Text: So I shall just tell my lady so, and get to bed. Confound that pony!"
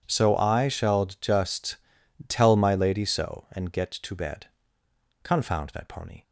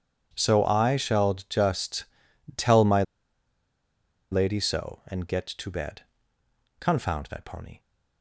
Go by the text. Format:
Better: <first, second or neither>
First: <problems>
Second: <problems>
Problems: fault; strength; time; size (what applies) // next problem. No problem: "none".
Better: first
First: pauses between "just" and "tell"; noticeable; at 1.7 s; 0.52 s long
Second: pauses between "just" and "tell"; noticeable; at 2.0 s; 0.52 s long // pauses between "my" and "lady"; strong; at 3.0 s; 1.2 s long